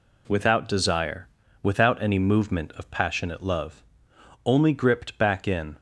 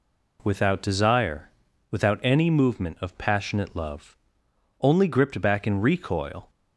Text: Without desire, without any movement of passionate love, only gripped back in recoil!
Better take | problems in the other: second | stops before "recoil"; at 5.7 s

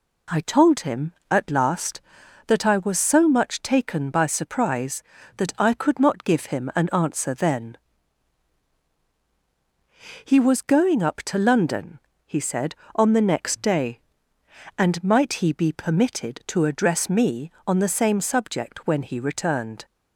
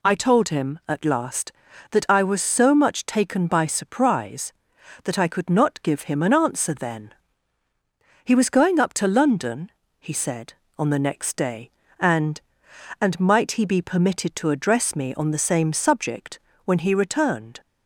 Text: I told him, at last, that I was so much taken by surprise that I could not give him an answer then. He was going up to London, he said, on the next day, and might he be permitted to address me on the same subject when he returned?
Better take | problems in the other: first | says "and" twice; at 13.0 s // pauses between "subject" and "when"; slight; at 16.3 s; 0.24 s long

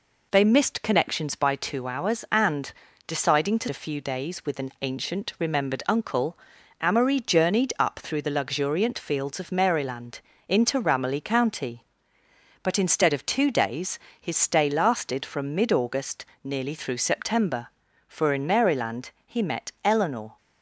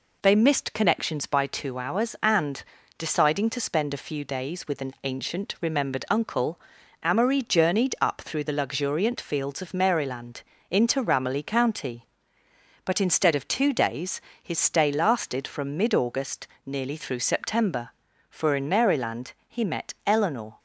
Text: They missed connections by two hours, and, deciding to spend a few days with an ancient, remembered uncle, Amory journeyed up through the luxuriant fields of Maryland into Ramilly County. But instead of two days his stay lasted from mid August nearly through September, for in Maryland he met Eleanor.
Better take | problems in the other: second | skips "spend"; at 3.6 s // pauses between "Maryland" and "into"; slight; at 10.2 s; 0.28 s long; slight in the second // pauses between "days" and "his"; slight; at 13.9 s; 0.22 s long; slight in the second // pauses between "August" and "nearly"; slight; at 16.2 s; 0.18 s long; slight in the second

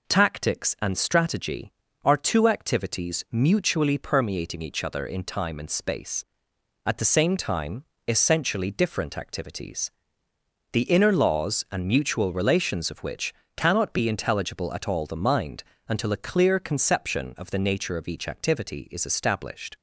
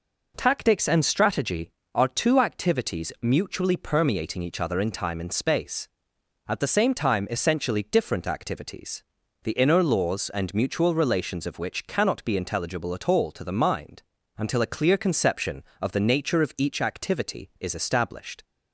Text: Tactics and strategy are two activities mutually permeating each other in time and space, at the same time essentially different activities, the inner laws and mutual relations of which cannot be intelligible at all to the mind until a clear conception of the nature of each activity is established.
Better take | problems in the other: second | pauses between "time" and "essentially"; slight; at 7.8 s; 0.24 s long // pauses between "which" and "cannot"; slight; at 13.3 s; 0.24 s long // skips "to"; at 15.0 s // pauses between "mind" and "until"; slight; at 15.6 s; 0.26 s long; slight in the second

